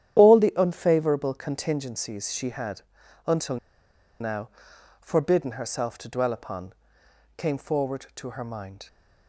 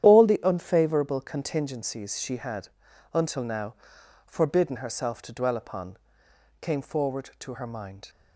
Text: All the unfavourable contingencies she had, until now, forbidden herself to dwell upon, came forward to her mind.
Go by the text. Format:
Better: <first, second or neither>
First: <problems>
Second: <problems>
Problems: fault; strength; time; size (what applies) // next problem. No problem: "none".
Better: second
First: starts louder than the rest; strong; until 1.2 s; 10.5 dB // pauses between "until" and "now"; noticeable; at 3.5 s; 0.64 s long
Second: starts louder than the rest; strong; until 1.0 s; 10.5 dB